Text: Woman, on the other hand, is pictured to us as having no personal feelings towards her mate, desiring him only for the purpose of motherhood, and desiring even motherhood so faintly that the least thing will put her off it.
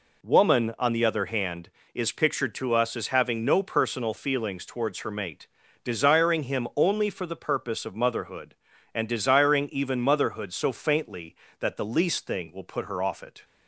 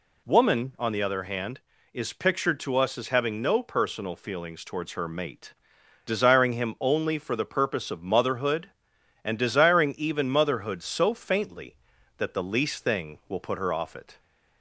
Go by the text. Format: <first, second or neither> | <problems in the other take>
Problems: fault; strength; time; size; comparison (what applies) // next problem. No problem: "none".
neither | none